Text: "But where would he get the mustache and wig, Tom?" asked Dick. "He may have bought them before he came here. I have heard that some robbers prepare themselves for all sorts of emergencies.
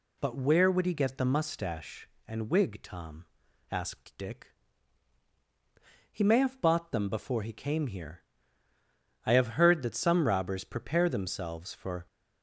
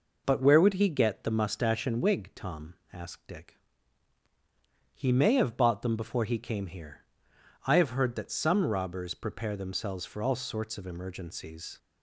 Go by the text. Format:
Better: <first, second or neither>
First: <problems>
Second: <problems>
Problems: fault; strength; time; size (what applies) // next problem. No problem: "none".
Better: second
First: stops before "all sorts of emergencies"; at 12.0 s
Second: none